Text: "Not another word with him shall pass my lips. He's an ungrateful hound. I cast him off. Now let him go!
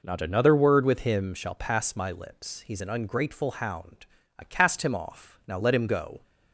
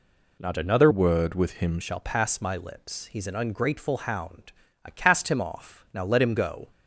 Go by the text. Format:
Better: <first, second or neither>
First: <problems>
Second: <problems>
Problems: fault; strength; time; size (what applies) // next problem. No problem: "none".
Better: first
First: none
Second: changes voice from "word" to "him"; from 0.9 to 1.7 s; 0.8 s long